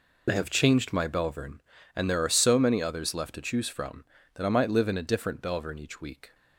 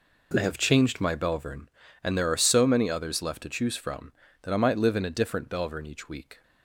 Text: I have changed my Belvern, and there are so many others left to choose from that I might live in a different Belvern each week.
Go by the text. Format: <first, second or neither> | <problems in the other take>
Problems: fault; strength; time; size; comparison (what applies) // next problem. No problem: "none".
second | loses the start of "I"; at 0.2 s; 45 ms